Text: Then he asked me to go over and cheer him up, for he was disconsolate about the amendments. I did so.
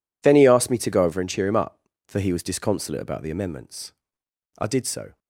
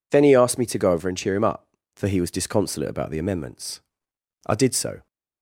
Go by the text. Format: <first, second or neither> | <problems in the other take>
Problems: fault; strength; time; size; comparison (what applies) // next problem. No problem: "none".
second | gets quieter; strong; throughout; 20 dB